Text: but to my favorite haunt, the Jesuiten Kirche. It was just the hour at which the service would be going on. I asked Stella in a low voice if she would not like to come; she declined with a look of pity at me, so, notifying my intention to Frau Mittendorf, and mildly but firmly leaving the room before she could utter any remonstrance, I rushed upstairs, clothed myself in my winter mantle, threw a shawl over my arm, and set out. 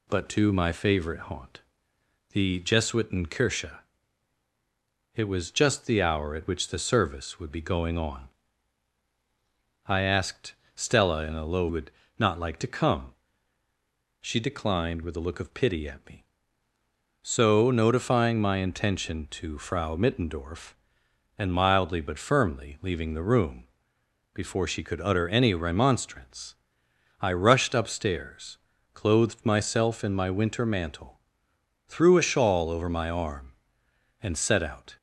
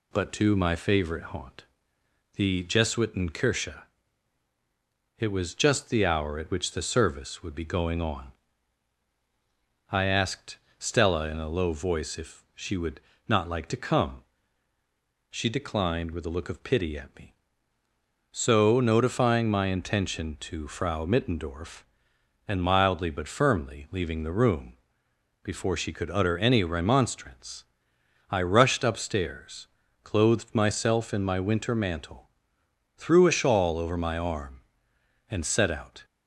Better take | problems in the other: second | pauses between "asked" and "Stella"; slight; at 10.5 s; 0.20 s long; slight in the second // skips "voice if she"; at 11.6 s // pauses between "would" and "not"; slight; at 11.9 s; 0.28 s long; slight in the second // pauses between "room" and "before"; noticeable; at 23.6 s; 0.68 s long; noticeable in the second

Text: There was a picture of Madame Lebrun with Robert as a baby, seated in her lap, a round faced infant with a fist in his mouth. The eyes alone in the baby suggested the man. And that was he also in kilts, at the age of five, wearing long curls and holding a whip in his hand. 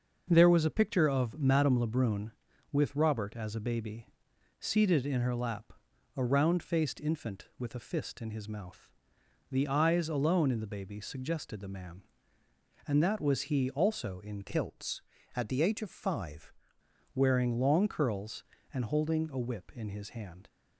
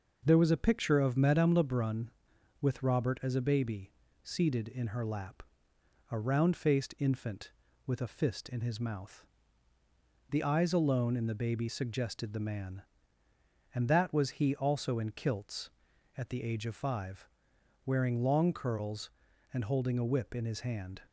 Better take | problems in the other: second | changes voice from "kilts" to "five"; from 14.4 to 16.5 s; 2.1 s long

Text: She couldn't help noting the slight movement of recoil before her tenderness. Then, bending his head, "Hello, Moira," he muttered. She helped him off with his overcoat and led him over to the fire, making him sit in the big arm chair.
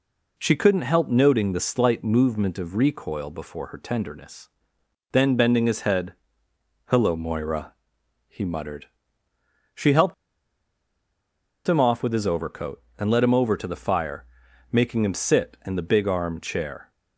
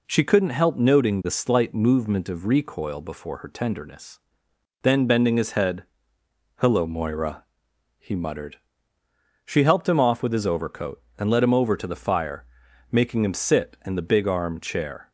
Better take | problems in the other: second | pauses between "helped" and "him"; strong; at 10.1 s; 1.5 s long

